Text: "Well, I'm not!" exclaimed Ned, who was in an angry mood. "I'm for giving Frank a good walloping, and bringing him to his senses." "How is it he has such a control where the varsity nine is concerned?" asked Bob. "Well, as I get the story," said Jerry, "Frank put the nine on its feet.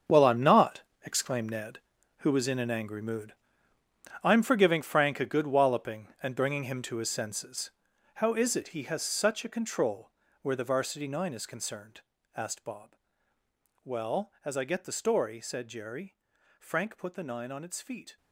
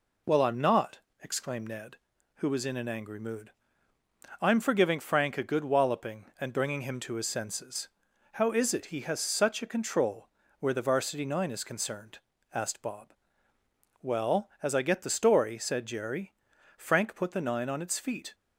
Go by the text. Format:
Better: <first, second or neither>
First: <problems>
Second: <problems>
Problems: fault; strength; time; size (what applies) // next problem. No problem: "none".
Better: second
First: gets quieter; strong; throughout; 12.5 dB // pauses between "control" and "where"; slight; at 10.1 s; 0.30 s long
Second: pauses between "control" and "where"; slight; at 10.2 s; 0.30 s long